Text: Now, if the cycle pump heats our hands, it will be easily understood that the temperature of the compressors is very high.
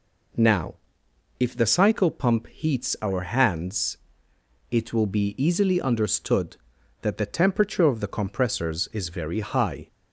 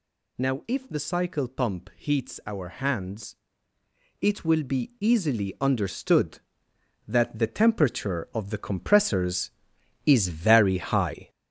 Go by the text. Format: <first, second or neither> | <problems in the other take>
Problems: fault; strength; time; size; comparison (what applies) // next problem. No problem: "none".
first | gets louder; throughout; 6.5 dB